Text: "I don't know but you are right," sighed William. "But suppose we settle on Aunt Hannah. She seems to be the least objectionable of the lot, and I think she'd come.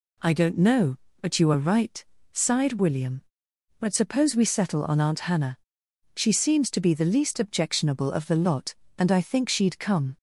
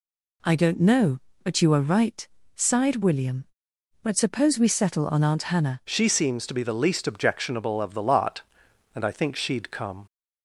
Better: first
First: none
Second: changes voice at "She"; from 5.8 s on; 4.2 s long

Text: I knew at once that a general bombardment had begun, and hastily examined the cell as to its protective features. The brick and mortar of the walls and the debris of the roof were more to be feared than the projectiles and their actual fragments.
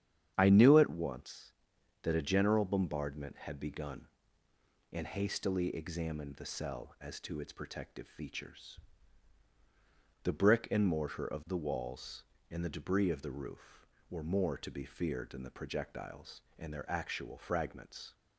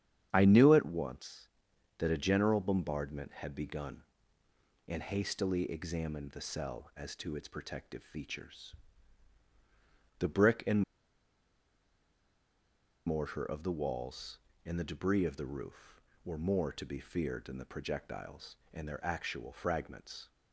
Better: first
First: starts louder than the rest; strong; until 1.3 s; 9 dB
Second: starts louder than the rest; strong; until 1.3 s; 9 dB // pauses between "and" and "mortar"; strong; at 10.8 s; 2.2 s long

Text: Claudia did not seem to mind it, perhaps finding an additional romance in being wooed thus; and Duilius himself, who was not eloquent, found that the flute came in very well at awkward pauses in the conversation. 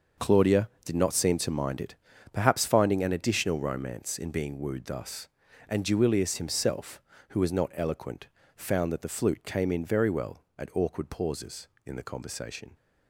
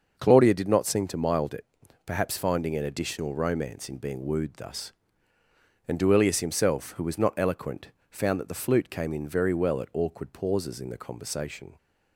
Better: first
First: starts louder than the rest; noticeable; until 1.3 s; 6 dB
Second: starts louder than the rest; until 1.2 s; 6 dB // says "mild" for "mind"; at 1.1 s

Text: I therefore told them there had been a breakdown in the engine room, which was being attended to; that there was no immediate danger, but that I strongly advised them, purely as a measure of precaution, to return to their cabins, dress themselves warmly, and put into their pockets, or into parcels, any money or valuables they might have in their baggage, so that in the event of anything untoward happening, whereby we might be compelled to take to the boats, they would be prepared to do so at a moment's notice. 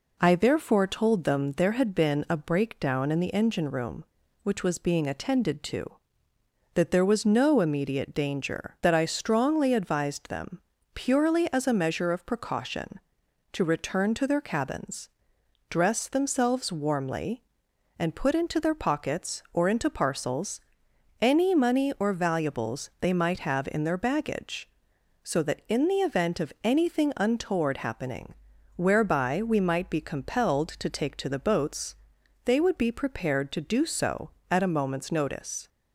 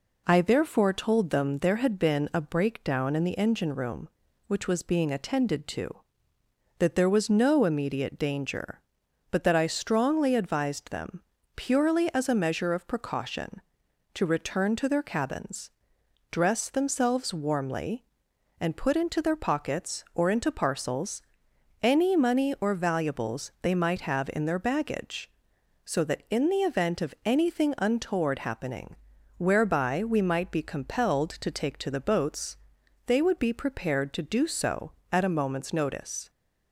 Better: second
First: skips "but"; at 8.8 s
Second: none

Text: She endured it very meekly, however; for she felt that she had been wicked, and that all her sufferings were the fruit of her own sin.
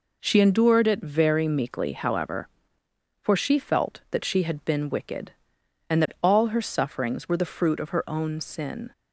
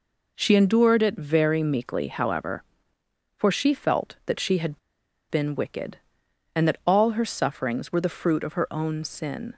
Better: first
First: none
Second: pauses between "had" and "been"; noticeable; at 4.7 s; 0.52 s long

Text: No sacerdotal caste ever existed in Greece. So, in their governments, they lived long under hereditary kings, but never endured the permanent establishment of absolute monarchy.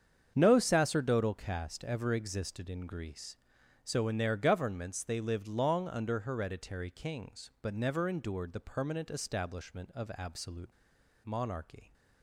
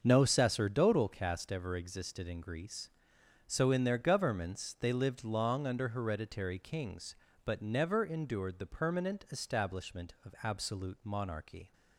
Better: second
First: starts louder than the rest; strong; until 1.3 s; 7.5 dB // pauses between "absolute" and "monarchy"; noticeable; at 10.6 s; 0.53 s long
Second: starts louder than the rest; until 1.0 s; 6.5 dB

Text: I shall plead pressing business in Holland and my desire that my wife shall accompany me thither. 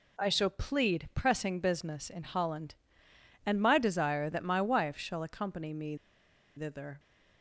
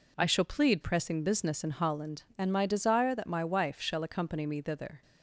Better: second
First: pauses between "me" and "thither"; noticeable; at 5.9 s; 0.61 s long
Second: none

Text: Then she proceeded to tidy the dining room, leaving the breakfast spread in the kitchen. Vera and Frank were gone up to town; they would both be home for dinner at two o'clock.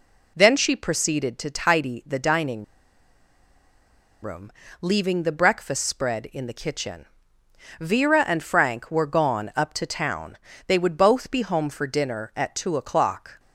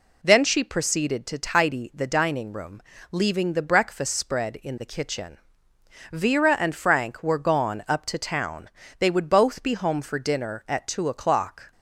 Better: second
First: pauses between "dining" and "room"; strong; at 2.6 s; 1.5 s long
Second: none

